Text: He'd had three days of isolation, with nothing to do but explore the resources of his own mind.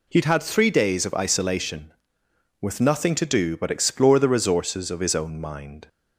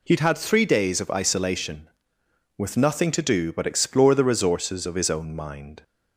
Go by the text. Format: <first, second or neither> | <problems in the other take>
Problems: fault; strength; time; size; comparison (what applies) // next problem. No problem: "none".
neither | none